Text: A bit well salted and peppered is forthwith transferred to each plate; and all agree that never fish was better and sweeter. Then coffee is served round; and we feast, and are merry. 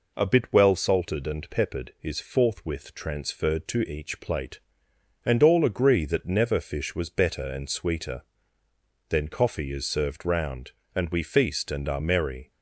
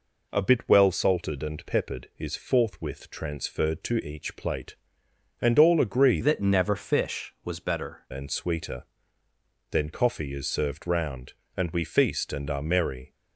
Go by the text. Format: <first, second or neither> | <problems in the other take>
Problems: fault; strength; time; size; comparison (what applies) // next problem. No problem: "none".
first | changes voice from "that" to "better"; from 6.2 to 8.0 s; 1.8 s long